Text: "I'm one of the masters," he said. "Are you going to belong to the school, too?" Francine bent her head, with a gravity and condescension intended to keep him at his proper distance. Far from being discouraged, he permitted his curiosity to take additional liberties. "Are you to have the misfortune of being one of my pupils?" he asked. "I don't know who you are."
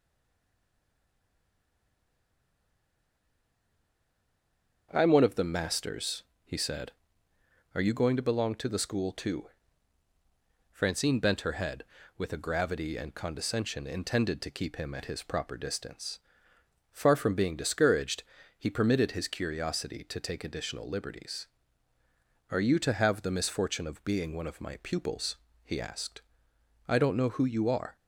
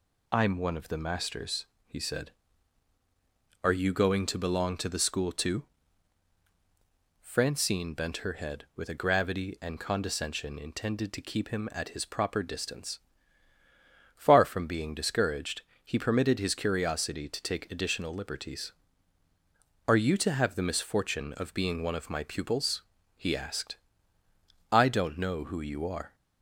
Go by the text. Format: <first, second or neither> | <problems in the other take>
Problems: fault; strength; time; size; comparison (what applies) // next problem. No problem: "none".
second | stays silent before the first word; strong; until 4.9 s; 4.9 s long // starts louder than the rest; until 5.9 s; 6.5 dB